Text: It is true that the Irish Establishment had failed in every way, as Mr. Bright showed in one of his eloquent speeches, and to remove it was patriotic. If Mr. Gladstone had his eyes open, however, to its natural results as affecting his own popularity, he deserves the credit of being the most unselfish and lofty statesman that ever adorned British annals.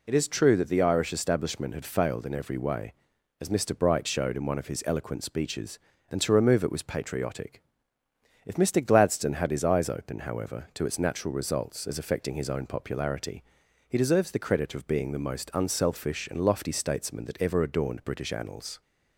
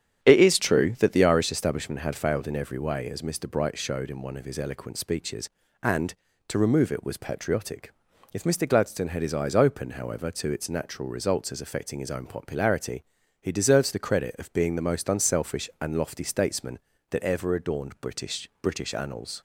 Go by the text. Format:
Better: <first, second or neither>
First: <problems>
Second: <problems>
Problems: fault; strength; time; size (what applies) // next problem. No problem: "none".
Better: first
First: none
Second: starts louder than the rest; strong; until 1.2 s; 9.5 dB // says "British" twice; at 18.6 s